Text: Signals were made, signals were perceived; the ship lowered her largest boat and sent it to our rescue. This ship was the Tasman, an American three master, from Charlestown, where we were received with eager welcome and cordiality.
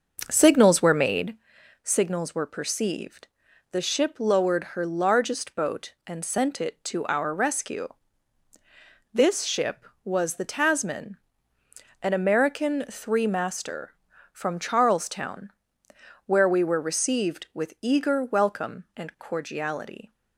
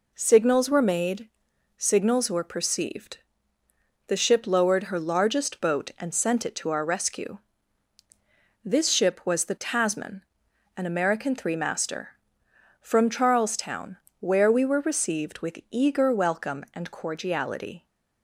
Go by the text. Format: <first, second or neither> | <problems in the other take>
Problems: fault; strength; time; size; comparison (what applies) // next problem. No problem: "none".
second | starts louder than the rest; noticeable; until 1.3 s; 6 dB